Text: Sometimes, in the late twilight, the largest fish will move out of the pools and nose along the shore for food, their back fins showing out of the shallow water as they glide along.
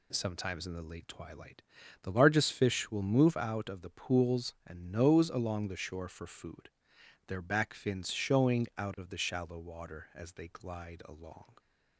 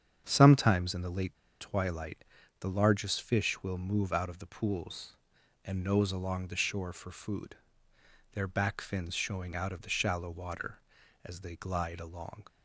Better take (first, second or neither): first